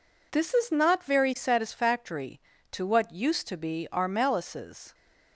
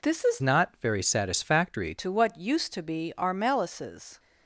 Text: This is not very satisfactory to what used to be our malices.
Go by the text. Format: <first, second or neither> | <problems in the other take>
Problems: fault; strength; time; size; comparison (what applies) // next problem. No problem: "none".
first | changes voice from "not" to "satisfactory"; from 0.4 to 1.9 s; 1.5 s long